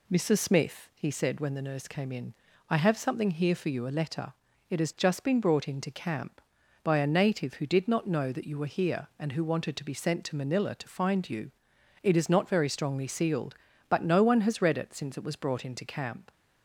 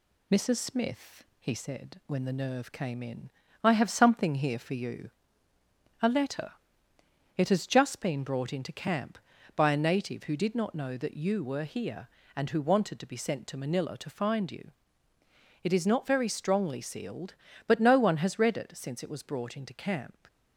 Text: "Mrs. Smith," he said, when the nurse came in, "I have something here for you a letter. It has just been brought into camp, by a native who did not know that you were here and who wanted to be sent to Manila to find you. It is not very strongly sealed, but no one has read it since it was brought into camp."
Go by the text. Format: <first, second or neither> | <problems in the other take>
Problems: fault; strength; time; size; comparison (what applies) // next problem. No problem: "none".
first | says "nerve" for "nurse"; at 2.3 s // pauses between "you" and "a"; noticeable; at 5.1 s; 0.90 s long